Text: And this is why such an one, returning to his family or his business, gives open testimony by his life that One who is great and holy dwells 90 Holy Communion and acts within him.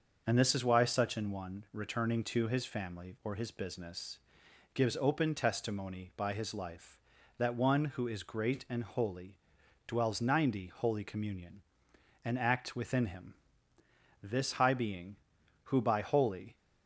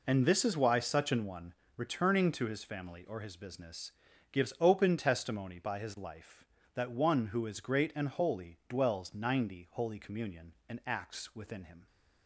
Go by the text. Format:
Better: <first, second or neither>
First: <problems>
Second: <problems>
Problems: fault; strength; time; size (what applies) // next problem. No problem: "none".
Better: second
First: starts louder than the rest; noticeable; until 1.2 s; 6 dB // pauses between "holy" and "dwells"; noticeable; at 9.3 s; 0.50 s long // goes on to say "This High Being who by Holy"; strong; from 14.2 s on; 2.3 s long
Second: none